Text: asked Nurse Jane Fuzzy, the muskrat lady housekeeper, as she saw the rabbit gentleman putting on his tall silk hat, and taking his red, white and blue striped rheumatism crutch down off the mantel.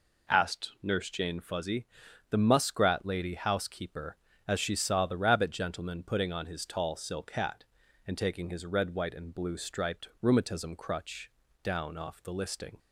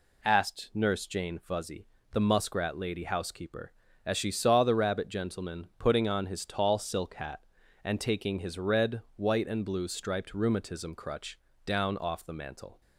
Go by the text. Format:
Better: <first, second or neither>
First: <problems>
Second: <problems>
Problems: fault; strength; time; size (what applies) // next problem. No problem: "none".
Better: second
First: pauses between "crutch" and "down"; slight; at 11.2 s; 0.32 s long // says "listing" for "mantel"; at 12.3 s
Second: pauses between "crutch" and "down"; slight; at 11.3 s; 0.26 s long